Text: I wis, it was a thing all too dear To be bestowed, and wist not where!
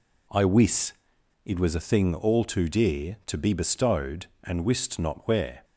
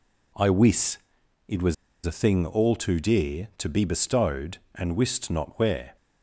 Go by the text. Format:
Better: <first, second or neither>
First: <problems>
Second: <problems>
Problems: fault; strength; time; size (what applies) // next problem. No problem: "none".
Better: first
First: none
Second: pauses between "was" and "a"; slight; at 1.7 s; 0.30 s long